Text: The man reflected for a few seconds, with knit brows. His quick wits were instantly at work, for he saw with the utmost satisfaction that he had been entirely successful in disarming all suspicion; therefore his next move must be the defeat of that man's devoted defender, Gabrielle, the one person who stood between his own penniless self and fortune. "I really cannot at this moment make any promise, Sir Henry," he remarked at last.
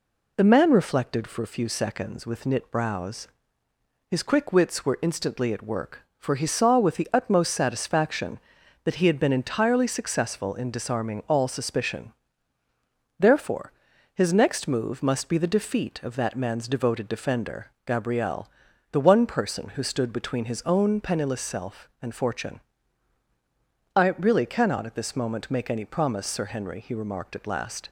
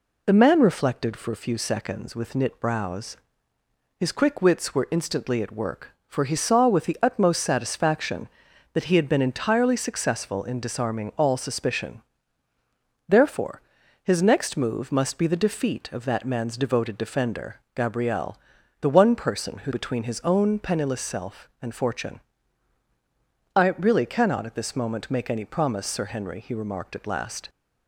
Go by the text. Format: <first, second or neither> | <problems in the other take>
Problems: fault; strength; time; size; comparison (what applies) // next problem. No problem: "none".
first | pauses between "therefore" and "his"; at 13.5 s; 0.42 s long; also in the first // skips "stood"; at 19.7 s